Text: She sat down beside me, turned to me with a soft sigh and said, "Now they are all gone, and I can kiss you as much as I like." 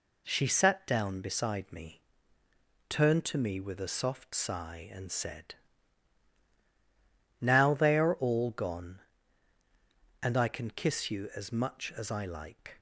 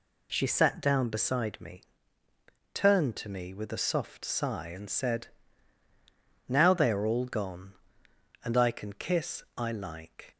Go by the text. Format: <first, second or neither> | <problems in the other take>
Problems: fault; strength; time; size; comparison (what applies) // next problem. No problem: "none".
first | skips "you as much as"; at 9.4 s